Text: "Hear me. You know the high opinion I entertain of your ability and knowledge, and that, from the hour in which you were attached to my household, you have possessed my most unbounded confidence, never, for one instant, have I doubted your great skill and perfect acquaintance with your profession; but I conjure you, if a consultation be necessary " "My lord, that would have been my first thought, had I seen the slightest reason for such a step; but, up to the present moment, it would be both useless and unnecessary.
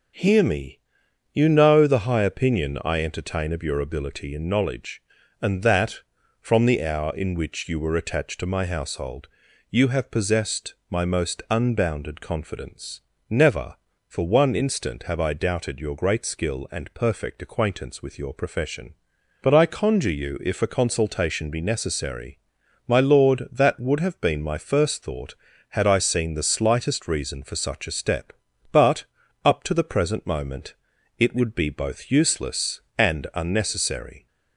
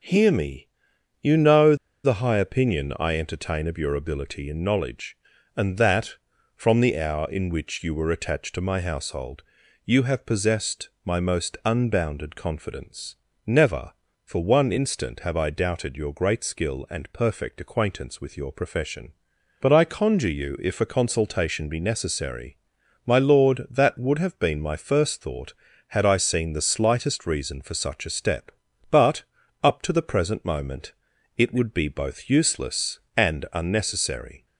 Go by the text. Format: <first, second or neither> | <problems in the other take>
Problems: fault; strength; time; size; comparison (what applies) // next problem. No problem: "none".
first | pauses between "know" and "the"; slight; at 1.7 s; 0.27 s long